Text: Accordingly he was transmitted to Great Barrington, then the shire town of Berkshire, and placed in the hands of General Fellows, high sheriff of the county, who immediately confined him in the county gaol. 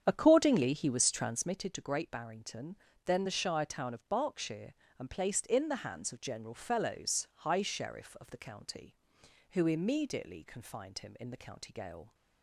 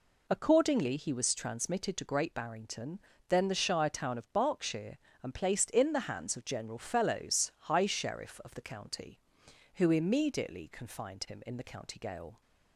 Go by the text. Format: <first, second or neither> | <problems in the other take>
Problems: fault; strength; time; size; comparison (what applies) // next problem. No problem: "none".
second | starts louder than the rest; strong; until 1.6 s; 8.5 dB